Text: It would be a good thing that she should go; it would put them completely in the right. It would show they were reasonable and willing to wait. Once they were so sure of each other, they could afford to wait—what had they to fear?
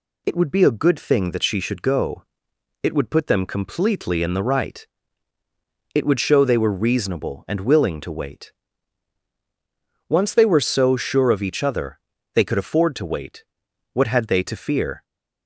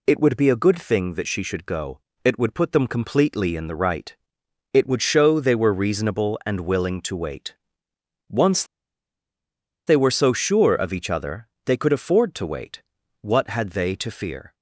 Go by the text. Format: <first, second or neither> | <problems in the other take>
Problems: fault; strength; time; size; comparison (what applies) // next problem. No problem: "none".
first | pauses between "Once" and "they"; at 8.6 s; 1.2 s long